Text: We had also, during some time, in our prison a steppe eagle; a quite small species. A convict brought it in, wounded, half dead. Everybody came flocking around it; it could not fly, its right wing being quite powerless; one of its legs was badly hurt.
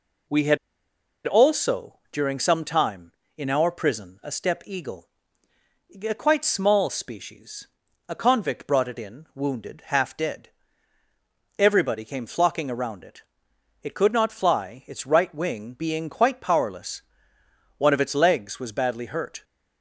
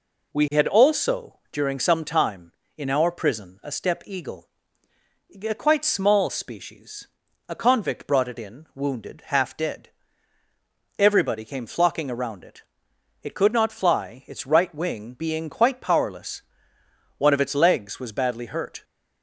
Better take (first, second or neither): second